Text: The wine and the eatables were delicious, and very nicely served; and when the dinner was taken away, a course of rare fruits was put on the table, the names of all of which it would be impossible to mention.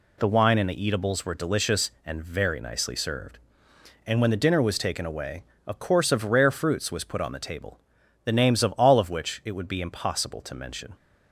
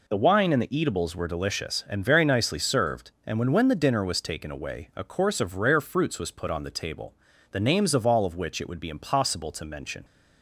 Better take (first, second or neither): first